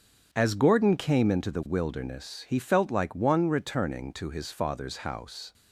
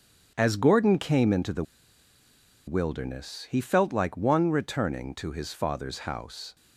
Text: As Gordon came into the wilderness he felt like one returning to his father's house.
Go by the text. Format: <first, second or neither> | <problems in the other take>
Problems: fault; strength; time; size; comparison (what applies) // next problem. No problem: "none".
first | starts louder than the rest; strong; until 1.3 s; 8 dB; strong in the first // pauses between "the" and "wilderness"; at 1.6 s; 1.0 s long